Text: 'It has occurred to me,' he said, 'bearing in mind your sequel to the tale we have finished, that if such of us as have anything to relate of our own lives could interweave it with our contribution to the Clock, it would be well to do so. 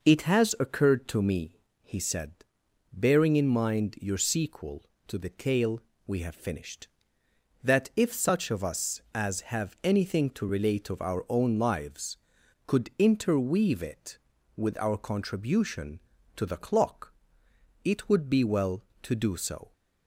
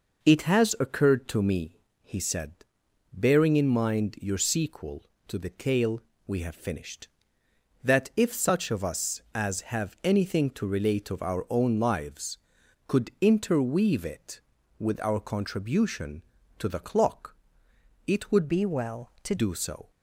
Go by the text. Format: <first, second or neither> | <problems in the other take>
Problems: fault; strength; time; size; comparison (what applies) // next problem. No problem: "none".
first | pauses between "tale" and "we"; slight; at 6.0 s; 0.26 s long; slight in the first // changes voice from "be" to "to"; from 18.4 to 19.3 s; 0.9 s long